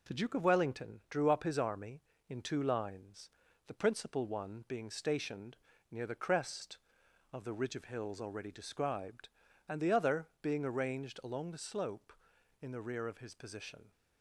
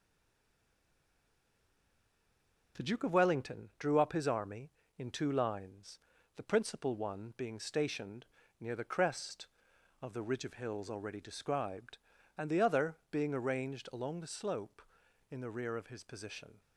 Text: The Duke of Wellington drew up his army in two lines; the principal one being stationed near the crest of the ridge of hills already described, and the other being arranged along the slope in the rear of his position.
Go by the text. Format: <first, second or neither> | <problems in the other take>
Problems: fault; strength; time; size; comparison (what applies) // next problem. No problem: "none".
first | stays silent before the first word; strong; until 2.7 s; 2.7 s long // pauses between "stationed" and "near"; slight; at 8.2 s; 0.34 s long; slight in the first